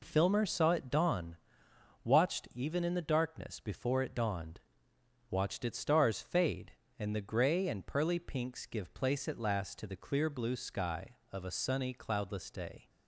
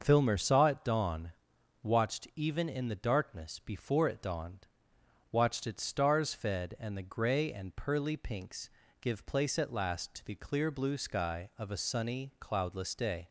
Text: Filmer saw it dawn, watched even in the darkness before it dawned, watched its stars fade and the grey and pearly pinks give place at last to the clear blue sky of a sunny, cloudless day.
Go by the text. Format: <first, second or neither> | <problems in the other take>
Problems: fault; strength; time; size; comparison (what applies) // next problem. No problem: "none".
first | starts louder than the rest; until 1.0 s; 6 dB // says "fed" for "fade"; at 6.3 s // pauses between "pinks" and "give"; slight; at 8.6 s; 0.32 s long